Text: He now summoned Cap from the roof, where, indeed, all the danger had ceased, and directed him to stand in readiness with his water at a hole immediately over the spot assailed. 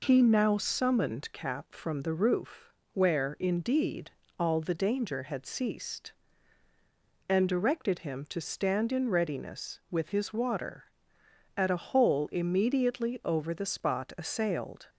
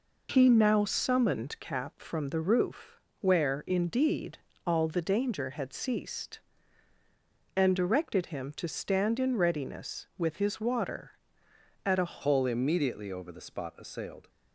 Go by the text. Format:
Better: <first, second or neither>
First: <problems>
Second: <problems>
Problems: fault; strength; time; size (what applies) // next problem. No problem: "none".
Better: first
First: none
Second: changes voice at "hole"; from 12.2 s on; 2.0 s long